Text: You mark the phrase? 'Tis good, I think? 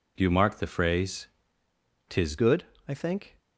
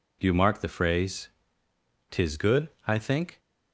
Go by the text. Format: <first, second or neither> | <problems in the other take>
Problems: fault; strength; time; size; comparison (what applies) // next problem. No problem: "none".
second | changes voice at "good"; from 2.3 s on; 1.0 s long